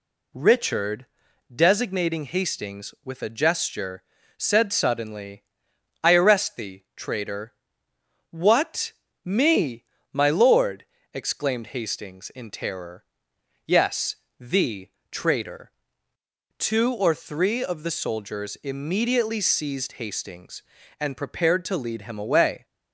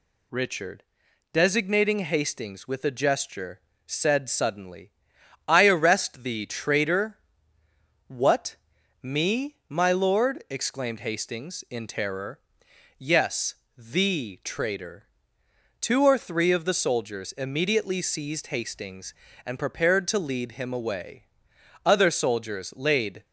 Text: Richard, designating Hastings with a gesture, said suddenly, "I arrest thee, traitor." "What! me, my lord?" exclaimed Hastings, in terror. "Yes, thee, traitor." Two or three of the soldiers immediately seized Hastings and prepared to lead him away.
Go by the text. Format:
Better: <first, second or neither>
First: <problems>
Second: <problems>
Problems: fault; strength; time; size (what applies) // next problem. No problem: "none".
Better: first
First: none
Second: goes on to say "Other soldiers laid"; from 21.8 s on; 1.4 s long